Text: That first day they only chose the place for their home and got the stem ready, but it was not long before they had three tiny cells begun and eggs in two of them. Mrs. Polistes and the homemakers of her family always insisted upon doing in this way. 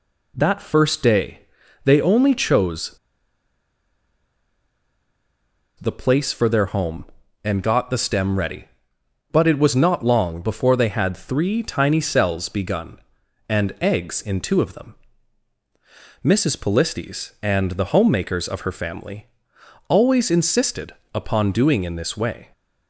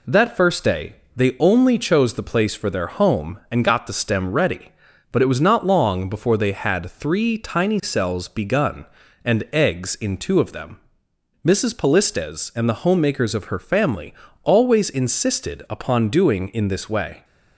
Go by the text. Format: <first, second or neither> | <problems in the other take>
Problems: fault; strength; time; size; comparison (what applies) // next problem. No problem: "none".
second | pauses between "day" and "they"; at 1.4 s; 0.44 s long; slight in the second // pauses between "chose" and "the"; strong; at 2.9 s; 2.8 s long // pauses between "family" and "always"; noticeable; at 19.2 s; 0.62 s long; slight in the second // pauses between "insisted" and "upon"; slight; at 20.9 s; 0.20 s long